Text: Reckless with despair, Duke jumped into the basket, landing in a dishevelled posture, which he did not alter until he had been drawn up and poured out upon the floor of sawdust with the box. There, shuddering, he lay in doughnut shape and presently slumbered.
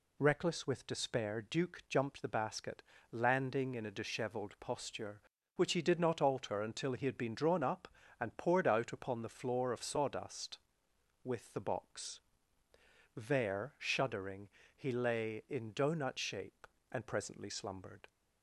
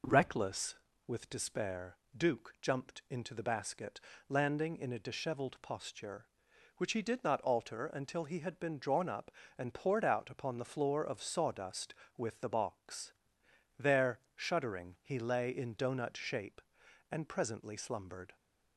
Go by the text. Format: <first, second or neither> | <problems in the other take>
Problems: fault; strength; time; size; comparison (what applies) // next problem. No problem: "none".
second | skips "into"; at 2.2 s